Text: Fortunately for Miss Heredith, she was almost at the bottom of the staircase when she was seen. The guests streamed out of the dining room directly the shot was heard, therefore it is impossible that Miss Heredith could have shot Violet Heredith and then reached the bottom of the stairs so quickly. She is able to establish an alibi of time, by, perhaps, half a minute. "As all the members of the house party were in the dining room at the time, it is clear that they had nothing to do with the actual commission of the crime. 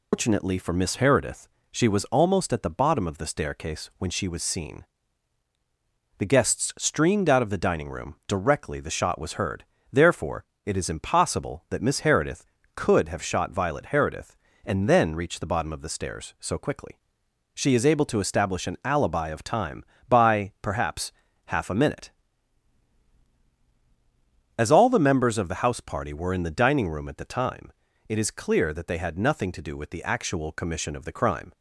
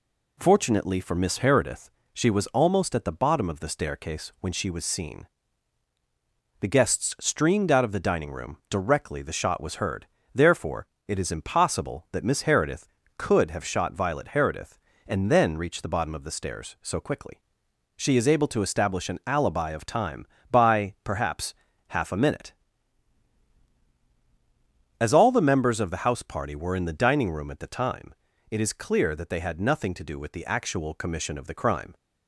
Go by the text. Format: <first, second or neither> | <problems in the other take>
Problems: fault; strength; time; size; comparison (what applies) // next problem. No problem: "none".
second | loses the start of "Fortunately"; at 0.1 s; 165 ms // pauses between "therefore" and "it"; slight; at 10.4 s; 0.22 s long; slight in the second